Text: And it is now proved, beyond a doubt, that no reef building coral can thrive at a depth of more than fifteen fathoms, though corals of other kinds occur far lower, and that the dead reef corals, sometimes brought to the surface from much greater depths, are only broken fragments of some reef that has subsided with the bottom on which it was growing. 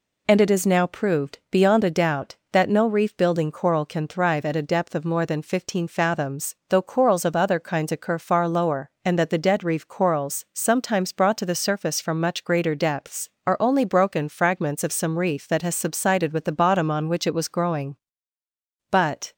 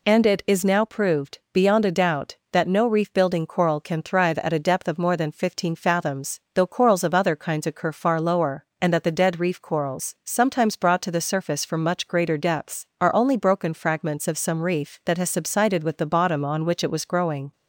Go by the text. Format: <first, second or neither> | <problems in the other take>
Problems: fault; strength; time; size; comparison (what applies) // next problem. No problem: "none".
second | goes on to say "But"; slight; from 18.9 s on; 0.42 s long